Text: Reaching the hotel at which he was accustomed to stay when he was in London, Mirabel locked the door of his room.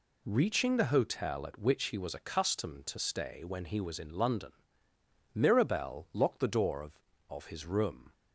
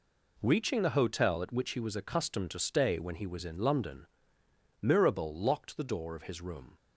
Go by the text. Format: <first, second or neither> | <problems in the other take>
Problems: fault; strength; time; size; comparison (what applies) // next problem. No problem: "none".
second | says "of" twice; at 7.2 s